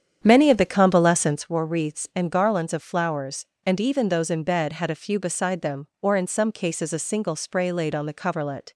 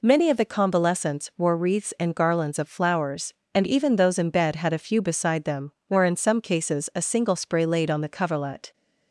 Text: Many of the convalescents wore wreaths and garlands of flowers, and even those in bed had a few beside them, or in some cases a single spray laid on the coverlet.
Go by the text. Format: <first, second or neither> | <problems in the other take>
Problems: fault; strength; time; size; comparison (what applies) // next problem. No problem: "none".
second | starts louder than the rest; strong; until 1.4 s; 8.5 dB